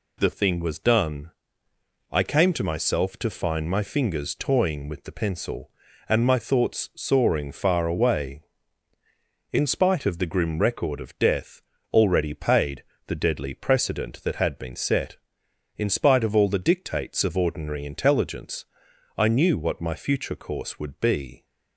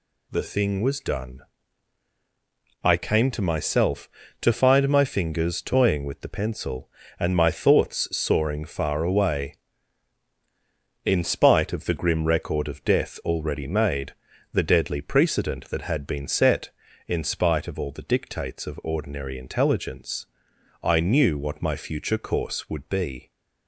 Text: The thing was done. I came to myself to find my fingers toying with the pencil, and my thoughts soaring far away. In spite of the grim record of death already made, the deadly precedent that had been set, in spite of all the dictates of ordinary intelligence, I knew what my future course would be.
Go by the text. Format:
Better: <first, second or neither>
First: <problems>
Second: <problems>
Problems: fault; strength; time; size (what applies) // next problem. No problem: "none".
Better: second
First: pauses between "death" and "already"; slight; at 11.6 s; 0.32 s long // says "paid" for "made"; at 12.3 s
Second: none